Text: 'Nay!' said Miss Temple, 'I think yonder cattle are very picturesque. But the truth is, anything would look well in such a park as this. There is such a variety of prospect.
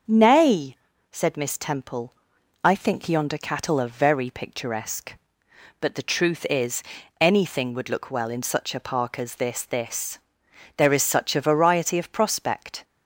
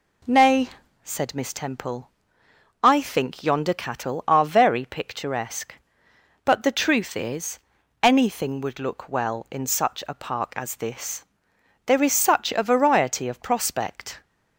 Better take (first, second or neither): second